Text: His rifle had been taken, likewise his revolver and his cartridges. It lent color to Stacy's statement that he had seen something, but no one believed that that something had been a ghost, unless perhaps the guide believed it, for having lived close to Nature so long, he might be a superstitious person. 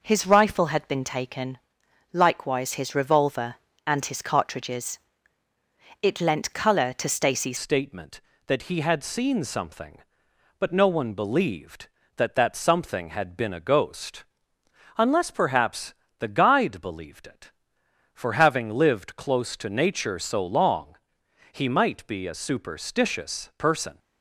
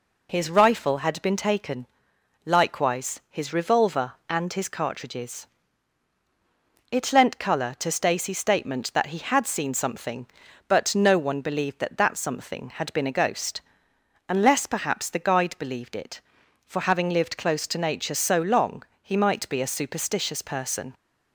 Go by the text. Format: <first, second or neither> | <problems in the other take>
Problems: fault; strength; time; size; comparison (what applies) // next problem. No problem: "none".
second | changes voice at "statement"; from 7.5 s on; 16.4 s long // pauses between "perhaps" and "the"; slight; at 15.9 s; 0.28 s long